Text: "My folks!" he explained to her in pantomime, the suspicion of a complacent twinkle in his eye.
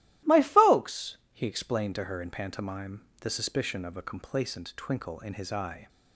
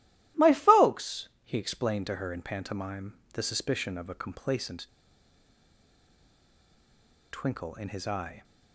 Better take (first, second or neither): first